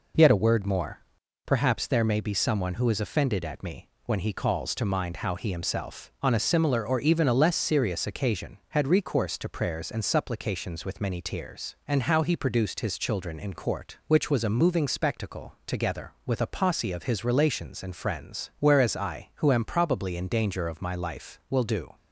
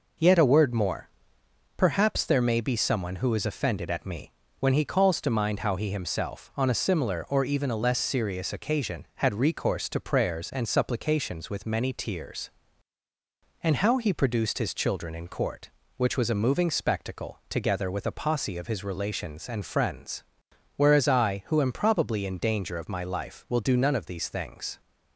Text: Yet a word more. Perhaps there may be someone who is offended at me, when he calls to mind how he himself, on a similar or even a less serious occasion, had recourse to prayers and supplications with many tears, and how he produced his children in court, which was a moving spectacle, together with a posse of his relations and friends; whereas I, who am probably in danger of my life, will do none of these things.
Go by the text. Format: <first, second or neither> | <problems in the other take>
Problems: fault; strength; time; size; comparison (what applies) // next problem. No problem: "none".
second | stops before "none of these things"; at 21.9 s